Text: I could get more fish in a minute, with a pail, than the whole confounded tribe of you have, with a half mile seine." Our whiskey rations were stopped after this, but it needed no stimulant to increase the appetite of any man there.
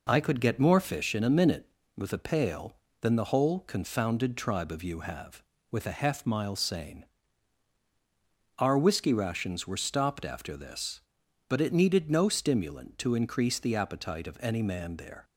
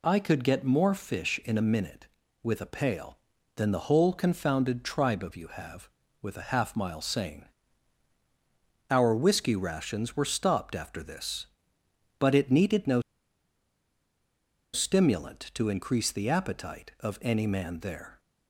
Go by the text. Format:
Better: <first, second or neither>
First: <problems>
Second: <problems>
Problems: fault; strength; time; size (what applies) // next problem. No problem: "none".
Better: first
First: none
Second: pauses between "no" and "stimulant"; strong; at 13.0 s; 1.7 s long